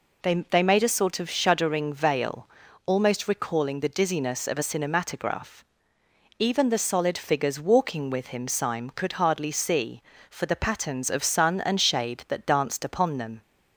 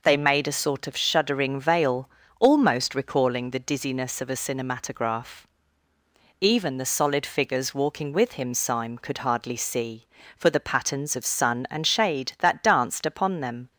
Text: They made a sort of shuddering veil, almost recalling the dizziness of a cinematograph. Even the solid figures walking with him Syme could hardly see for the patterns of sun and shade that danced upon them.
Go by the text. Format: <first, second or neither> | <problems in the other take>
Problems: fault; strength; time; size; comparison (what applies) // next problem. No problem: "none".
second | says "They" twice; at 0.4 s